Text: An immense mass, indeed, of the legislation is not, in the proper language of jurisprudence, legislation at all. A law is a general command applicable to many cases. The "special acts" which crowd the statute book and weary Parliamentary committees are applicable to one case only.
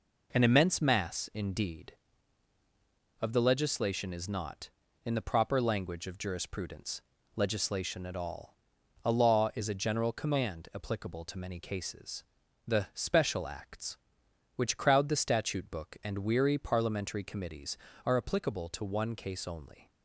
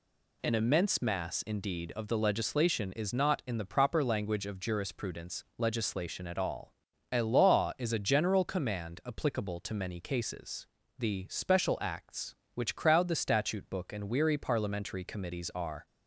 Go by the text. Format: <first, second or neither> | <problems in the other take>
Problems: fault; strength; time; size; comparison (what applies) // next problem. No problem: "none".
first | stops before "applicable to one case only"; at 15.8 s